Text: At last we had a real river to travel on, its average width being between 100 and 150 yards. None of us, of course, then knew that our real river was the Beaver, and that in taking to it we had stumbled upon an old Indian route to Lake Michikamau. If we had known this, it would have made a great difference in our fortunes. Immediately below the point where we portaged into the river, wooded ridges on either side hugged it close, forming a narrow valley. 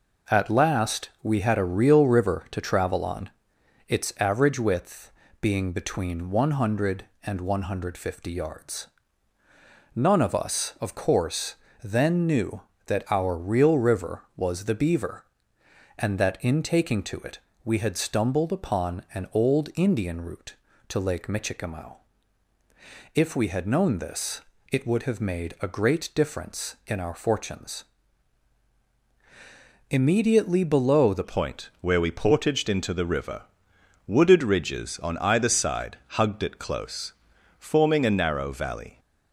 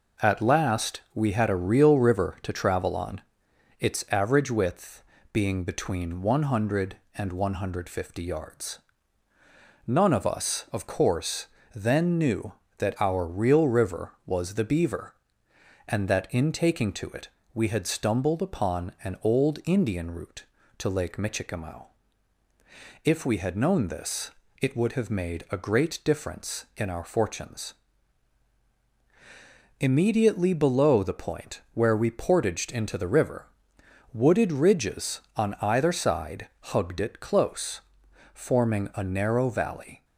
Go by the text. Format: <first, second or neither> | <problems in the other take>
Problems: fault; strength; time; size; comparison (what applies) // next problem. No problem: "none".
second | pauses between "width" and "being"; slight; at 5.1 s; 0.30 s long; slight in the second // pauses between "it" and "we"; slight; at 17.3 s; 0.24 s long; slight in the second // changes voice at "point"; from 31.2 s on; 7.7 s long